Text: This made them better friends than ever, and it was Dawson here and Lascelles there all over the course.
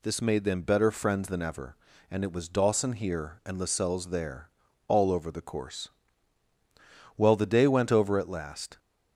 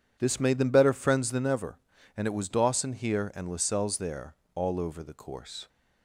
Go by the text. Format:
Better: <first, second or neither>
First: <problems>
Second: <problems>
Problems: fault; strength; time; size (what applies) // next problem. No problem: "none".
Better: second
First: pauses between "there" and "all"; at 4.4 s; 0.40 s long // goes on to say "Well the day went over at last"; from 7.1 s on; 1.6 s long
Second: pauses between "there" and "all"; slight; at 4.3 s; 0.18 s long